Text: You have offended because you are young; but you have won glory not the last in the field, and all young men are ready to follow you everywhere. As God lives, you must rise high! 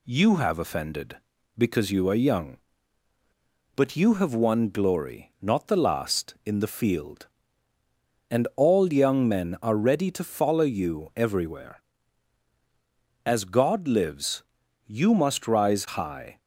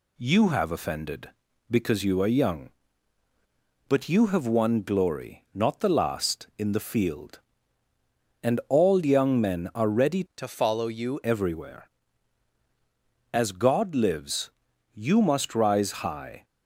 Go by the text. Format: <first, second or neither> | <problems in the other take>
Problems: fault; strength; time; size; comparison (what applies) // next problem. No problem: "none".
first | changes voice from "to" to "you"; from 10.3 to 11.1 s; 0.8 s long